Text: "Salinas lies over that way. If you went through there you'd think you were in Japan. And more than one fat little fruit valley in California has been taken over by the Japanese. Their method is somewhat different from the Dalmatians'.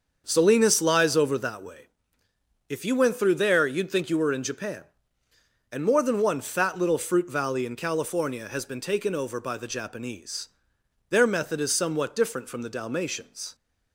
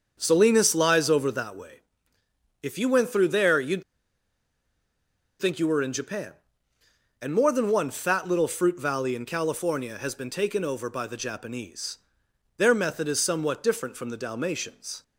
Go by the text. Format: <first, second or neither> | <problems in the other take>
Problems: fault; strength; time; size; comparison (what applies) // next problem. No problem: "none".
first | starts louder than the rest; until 1.2 s; 6.5 dB; also in the first // pauses between "you'd" and "think"; strong; at 3.8 s; 1.5 s long